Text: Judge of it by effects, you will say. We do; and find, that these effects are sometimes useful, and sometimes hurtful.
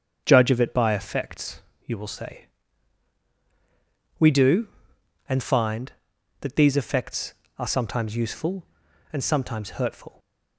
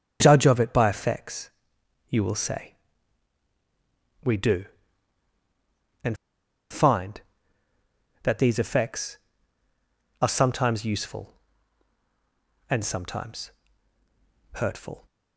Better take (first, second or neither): first